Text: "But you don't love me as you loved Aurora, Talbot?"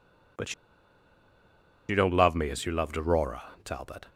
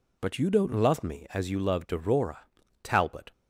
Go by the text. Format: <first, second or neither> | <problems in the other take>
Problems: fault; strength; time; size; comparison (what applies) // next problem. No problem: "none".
second | pauses between "But" and "you"; strong; at 0.5 s; 1.3 s long